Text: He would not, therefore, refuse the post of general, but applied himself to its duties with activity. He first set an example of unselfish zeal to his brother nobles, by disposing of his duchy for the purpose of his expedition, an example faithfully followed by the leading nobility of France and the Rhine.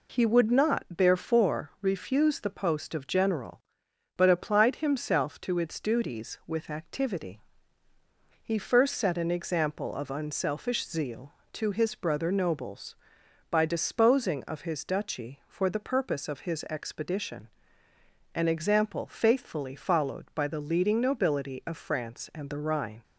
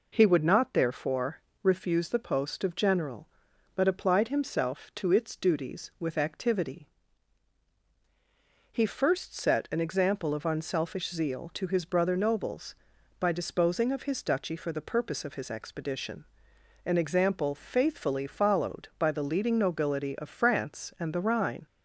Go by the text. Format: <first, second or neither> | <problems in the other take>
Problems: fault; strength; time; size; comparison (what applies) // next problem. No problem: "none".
neither | none